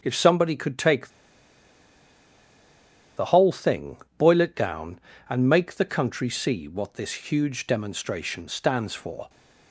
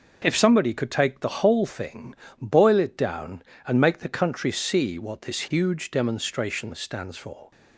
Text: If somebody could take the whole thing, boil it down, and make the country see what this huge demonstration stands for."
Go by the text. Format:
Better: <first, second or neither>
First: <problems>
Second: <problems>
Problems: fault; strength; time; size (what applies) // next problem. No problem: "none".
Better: second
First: starts louder than the rest; strong; until 1.0 s; 7.5 dB // pauses between "take" and "the"; strong; at 1.0 s; 2.0 s long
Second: none